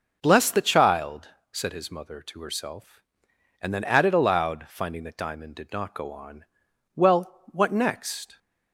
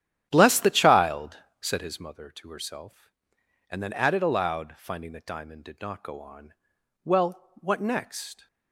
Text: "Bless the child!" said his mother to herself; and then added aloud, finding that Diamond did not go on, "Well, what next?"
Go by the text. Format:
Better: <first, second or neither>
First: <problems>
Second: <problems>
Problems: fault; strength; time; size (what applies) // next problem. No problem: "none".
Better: first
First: none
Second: starts louder than the rest; strong; until 2.2 s; 11 dB